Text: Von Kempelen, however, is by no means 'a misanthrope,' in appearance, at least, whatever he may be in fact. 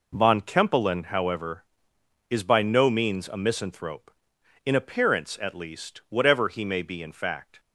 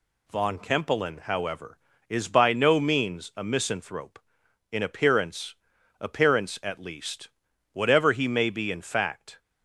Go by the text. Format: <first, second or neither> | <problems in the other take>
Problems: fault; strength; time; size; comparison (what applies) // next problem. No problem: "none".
first | says "appearance" twice; at 6.0 s